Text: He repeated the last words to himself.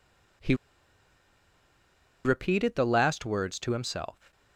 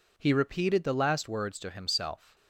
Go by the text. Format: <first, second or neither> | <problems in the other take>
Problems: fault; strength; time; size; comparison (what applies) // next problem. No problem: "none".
second | pauses between "He" and "repeated"; strong; at 0.5 s; 1.6 s long